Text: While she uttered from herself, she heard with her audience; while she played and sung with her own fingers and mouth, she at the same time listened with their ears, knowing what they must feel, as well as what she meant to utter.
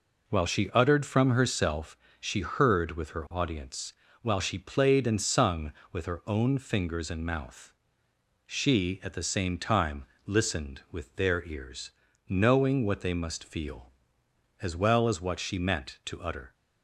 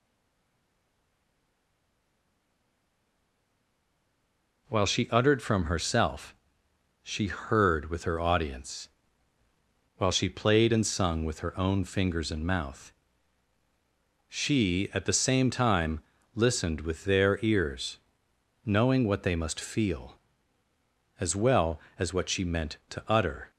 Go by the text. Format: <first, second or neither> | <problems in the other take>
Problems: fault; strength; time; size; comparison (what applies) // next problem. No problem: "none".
first | stays silent before the first word; strong; until 4.6 s; 4.6 s long // pauses between "time" and "listened"; slight; at 16.0 s; 0.36 s long; slight in the first